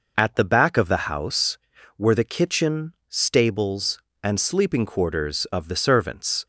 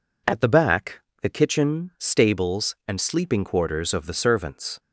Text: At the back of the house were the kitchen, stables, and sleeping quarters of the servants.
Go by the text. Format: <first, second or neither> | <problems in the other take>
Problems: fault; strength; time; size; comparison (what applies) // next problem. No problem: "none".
first | skips "of the house were"; at 1.1 s